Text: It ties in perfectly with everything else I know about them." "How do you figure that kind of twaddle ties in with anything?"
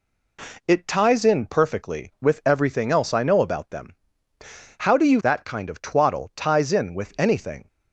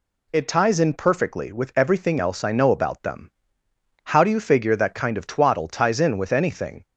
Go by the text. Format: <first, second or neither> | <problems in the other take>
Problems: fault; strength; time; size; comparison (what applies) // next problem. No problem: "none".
second | skips "figure"; at 5.1 s